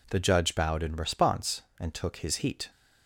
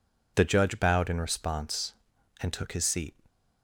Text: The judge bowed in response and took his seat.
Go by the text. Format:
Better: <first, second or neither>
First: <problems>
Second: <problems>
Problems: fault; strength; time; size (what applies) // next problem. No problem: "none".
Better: second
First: says "heat" for "seat"; at 2.3 s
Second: none